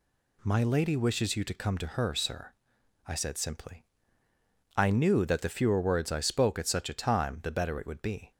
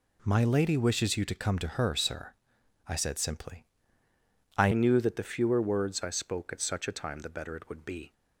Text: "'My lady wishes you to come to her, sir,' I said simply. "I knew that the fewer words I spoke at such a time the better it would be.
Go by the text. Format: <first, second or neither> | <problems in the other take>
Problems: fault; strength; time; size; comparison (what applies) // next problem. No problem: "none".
first | changes voice at "knew"; from 4.7 s on; 3.4 s long